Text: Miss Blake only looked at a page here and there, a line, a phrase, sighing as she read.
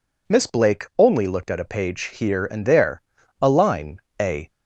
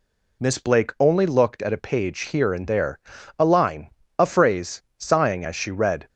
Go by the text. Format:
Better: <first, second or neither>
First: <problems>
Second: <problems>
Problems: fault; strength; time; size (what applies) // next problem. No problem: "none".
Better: second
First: stops before "phrase sighing as she read"; at 4.4 s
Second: none